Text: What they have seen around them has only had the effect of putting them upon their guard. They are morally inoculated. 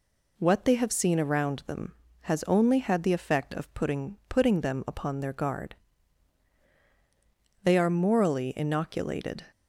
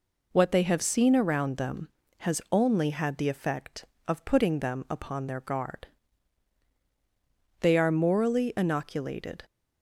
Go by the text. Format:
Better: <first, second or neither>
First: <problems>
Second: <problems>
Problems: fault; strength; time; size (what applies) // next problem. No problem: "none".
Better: second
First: says "putting" twice; at 4.2 s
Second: none